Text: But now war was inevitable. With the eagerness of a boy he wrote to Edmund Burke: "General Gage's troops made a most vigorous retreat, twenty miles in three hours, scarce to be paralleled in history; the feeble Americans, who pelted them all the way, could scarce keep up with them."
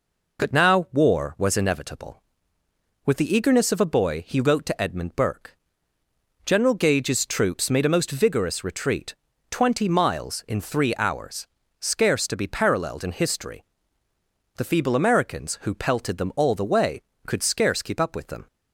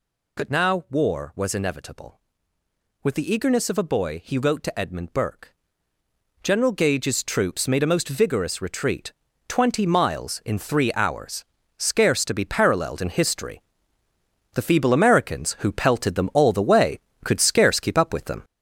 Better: first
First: none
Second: gets louder; throughout; 6.5 dB

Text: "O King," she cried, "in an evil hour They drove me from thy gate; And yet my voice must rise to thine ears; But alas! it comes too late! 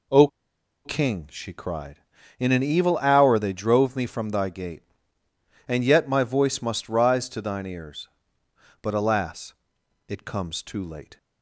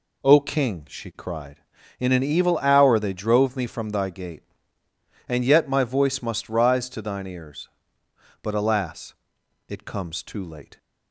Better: second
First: pauses between "O" and "King"; noticeable; at 0.2 s; 0.56 s long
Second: none

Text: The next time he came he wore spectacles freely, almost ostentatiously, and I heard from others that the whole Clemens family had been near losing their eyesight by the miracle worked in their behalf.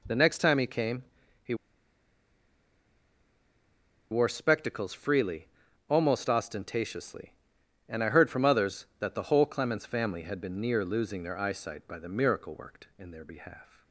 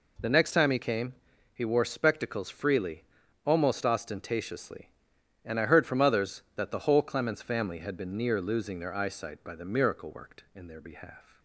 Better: second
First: pauses between "came" and "he"; at 1.0 s; 0.40 s long // pauses between "he" and "wore"; strong; at 1.5 s; 2.5 s long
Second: pauses between "came" and "he"; at 1.1 s; 0.40 s long

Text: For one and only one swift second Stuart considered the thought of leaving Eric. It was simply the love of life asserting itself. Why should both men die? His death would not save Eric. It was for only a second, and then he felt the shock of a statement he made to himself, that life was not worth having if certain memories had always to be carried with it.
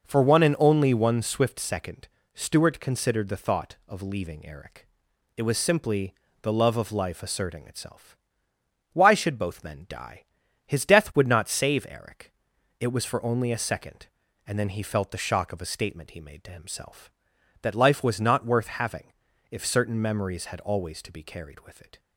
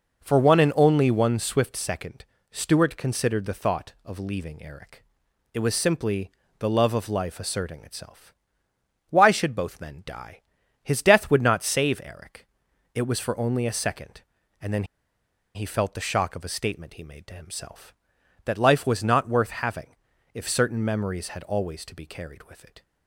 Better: first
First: pauses between "second" and "Stuart"; slight; at 2.0 s; 0.26 s long // pauses between "simply" and "the"; slight; at 6.1 s; 0.26 s long // pauses between "having" and "if"; slight; at 19.1 s; 0.36 s long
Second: pauses between "second" and "Stuart"; slight; at 2.2 s; 0.26 s long // pauses between "simply" and "the"; slight; at 6.3 s; 0.26 s long // pauses between "then" and "he"; noticeable; at 14.8 s; 0.71 s long // pauses between "having" and "if"; slight; at 19.9 s; 0.36 s long

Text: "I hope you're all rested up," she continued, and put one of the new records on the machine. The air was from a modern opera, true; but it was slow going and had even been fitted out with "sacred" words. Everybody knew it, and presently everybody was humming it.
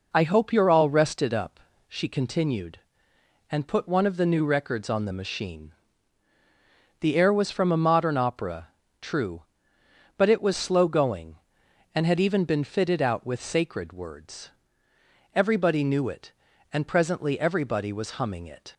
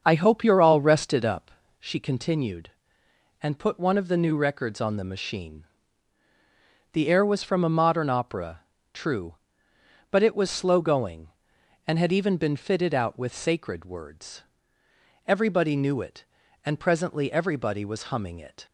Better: first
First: none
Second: starts louder than the rest; until 1.7 s; 7 dB

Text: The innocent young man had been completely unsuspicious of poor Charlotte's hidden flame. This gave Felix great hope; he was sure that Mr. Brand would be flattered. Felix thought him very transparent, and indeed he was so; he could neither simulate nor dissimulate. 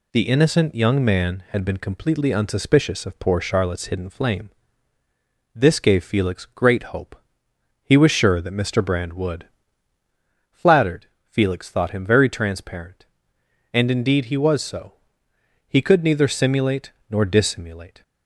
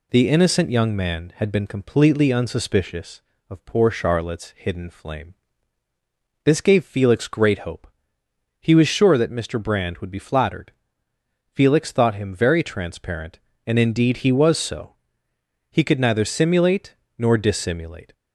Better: second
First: skips "be"; at 9.9 s // pauses between "simulate" and "nor"; slight; at 16.9 s; 0.20 s long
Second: pauses between "simulate" and "nor"; slight; at 16.9 s; 0.20 s long

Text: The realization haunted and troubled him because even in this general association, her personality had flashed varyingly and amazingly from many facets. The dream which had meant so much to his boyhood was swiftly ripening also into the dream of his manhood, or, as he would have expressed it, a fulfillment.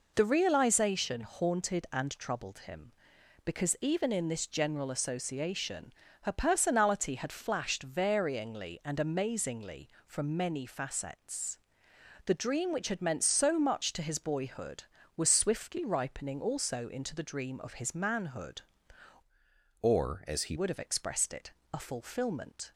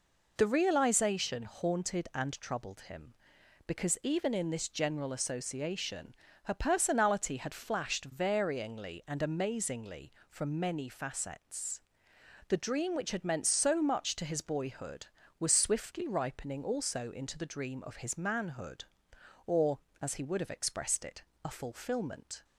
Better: second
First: changes voice from "or" to "he"; from 19.8 to 20.5 s; 0.7 s long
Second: none

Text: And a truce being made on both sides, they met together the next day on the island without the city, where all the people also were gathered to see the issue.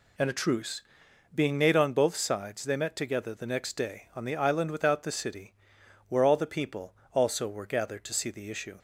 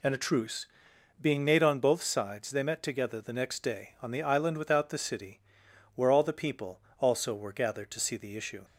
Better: neither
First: pauses between "truce" and "being"; noticeable; at 0.8 s; 0.52 s long // pauses between "people" and "also"; slight; at 6.9 s; 0.19 s long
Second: pauses between "truce" and "being"; noticeable; at 0.6 s; 0.54 s long // pauses between "people" and "also"; slight; at 6.7 s; 0.18 s long

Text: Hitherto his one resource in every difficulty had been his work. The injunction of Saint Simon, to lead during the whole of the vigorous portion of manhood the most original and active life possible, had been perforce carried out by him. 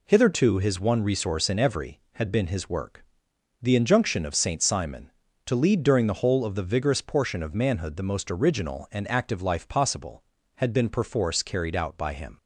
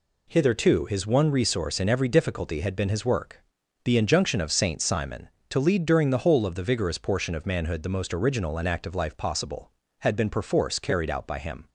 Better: second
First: skips "difficulty"; at 2.0 s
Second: none

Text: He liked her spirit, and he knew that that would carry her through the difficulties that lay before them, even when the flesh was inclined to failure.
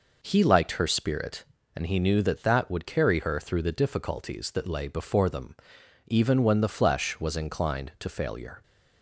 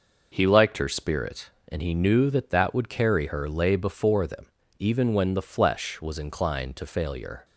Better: first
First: none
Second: skips "through the difficulties that"; at 3.4 s

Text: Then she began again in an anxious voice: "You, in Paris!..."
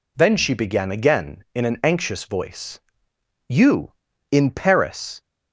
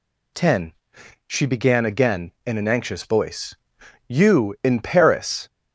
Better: first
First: none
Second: says "Ten" for "Then"; at 0.3 s

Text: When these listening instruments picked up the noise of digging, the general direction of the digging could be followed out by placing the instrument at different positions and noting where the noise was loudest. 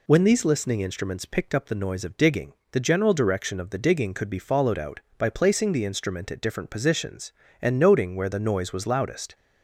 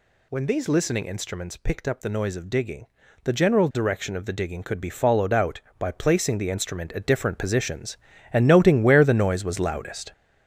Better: first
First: none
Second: gets louder; throughout; 7 dB

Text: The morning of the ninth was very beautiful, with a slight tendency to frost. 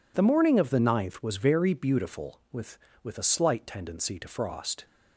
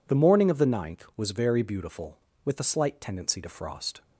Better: second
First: says "with" twice; at 3.0 s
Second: none

